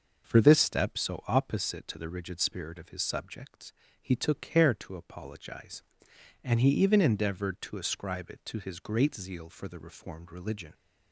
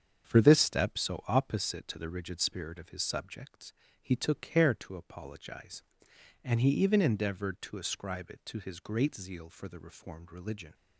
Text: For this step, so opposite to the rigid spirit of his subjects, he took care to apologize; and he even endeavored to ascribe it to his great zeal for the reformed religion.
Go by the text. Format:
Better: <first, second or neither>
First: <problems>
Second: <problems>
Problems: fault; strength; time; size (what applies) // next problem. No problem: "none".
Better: first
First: none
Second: gets quieter; throughout; 7 dB